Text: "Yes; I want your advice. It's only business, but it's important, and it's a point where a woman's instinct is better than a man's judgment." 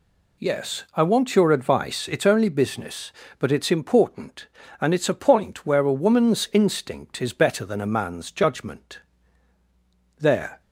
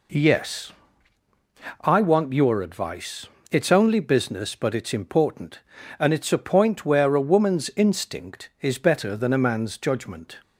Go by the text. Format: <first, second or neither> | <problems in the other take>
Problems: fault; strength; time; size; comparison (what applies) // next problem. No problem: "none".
second | goes on to say "There"; slight; from 10.1 s on; 0.44 s long